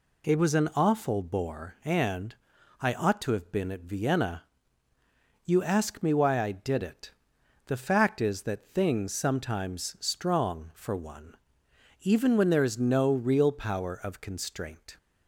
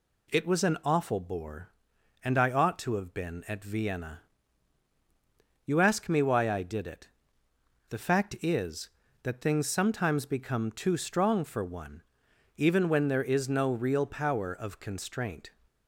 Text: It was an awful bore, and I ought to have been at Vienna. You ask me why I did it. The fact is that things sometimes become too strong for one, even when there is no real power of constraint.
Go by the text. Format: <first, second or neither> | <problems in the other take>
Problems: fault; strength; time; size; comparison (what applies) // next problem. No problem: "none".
second | pauses between "and" and "I"; noticeable; at 2.3 s; 0.48 s long // skips "become too"; at 9.9 s